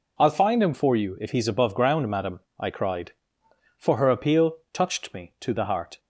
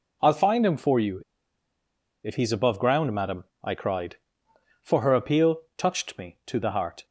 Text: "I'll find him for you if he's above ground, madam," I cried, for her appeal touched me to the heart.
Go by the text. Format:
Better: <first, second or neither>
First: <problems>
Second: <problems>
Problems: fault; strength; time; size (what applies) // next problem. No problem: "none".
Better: first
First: none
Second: pauses between "you" and "if"; at 1.2 s; 1.0 s long